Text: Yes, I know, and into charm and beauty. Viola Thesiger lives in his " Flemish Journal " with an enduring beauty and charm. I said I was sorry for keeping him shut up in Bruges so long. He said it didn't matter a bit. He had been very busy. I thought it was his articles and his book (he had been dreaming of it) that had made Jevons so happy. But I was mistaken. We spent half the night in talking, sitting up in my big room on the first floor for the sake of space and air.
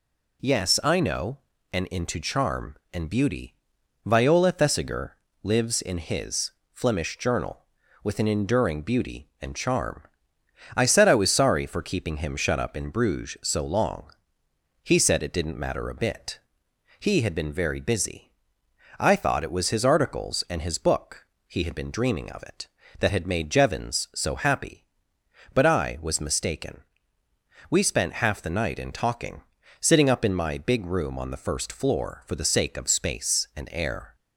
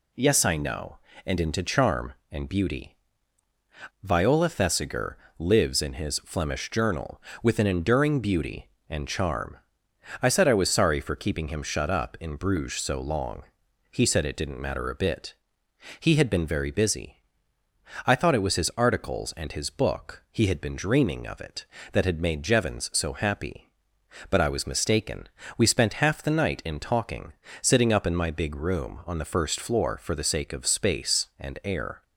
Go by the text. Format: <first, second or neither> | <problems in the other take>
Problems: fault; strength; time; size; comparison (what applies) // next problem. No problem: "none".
neither | pauses between "Thesiger" and "lives"; slight; the same in both